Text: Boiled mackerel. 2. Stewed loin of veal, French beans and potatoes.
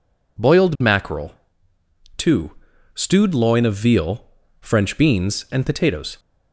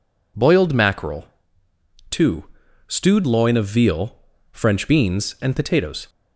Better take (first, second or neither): neither